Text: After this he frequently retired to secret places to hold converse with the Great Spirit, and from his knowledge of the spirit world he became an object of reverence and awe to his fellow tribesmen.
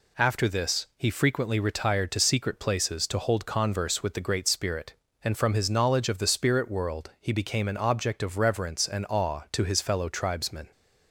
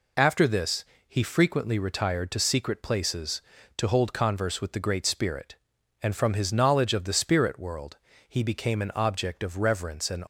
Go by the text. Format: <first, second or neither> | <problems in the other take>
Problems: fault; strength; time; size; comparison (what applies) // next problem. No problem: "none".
first | pauses between "this" and "he"; slight; at 0.8 s; 0.22 s long // pauses between "world" and "he"; slight; at 7.9 s; 0.32 s long // stops before "awe to his fellow tribesmen"; at 10.2 s